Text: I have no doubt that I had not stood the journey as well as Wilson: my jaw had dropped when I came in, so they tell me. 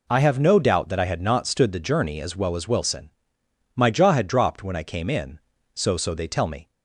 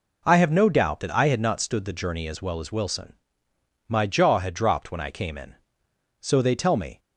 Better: second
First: says "so" twice; at 5.9 s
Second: none

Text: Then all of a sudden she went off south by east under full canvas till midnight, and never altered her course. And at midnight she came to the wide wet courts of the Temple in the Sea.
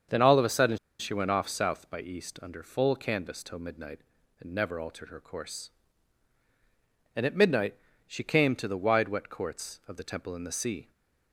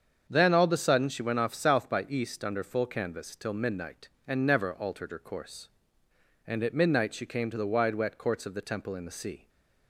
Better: second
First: starts louder than the rest; until 1.3 s; 7 dB // pauses between "sudden" and "she"; slight; at 0.7 s; 0.23 s long // pauses between "midnight" and "she"; slight; at 7.7 s; 0.32 s long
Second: starts louder than the rest; strong; until 1.3 s; 7 dB

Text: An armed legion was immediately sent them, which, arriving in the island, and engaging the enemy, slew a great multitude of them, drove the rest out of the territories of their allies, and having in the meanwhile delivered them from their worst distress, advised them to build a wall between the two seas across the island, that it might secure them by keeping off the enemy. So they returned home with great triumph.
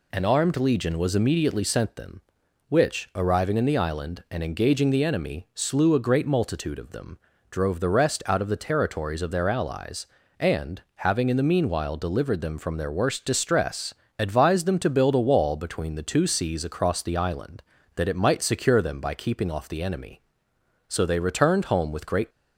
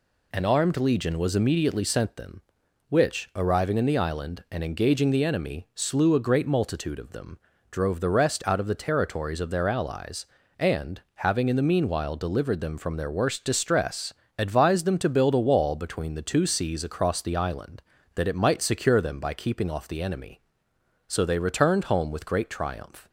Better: second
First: stops before "triumph"; at 22.2 s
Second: none

